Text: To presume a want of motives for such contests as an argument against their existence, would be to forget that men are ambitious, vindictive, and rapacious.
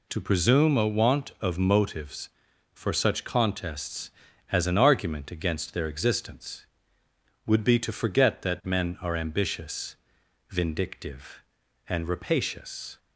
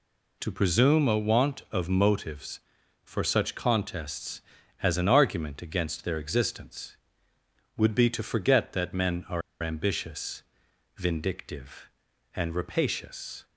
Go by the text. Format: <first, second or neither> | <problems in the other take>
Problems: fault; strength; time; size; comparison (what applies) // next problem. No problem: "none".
first | pauses between "are" and "ambitious"; slight; at 9.4 s; 0.20 s long